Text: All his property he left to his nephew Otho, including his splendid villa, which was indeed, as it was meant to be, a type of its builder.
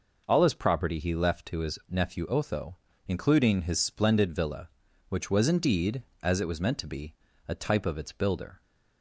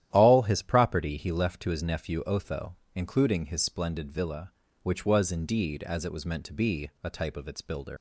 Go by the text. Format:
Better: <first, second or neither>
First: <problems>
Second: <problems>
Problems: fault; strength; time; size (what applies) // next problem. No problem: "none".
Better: first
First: none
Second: starts louder than the rest; strong; until 1.1 s; 12 dB // leaves "builder" unfinished; at 7.9 s; 100 ms